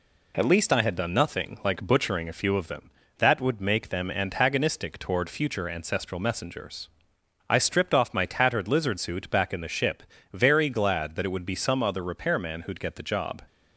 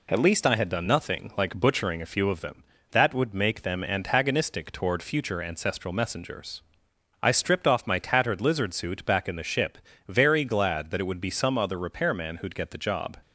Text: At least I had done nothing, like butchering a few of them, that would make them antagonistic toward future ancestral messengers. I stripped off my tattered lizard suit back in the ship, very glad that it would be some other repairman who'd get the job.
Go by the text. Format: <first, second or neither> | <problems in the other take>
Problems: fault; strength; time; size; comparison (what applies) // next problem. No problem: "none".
neither | none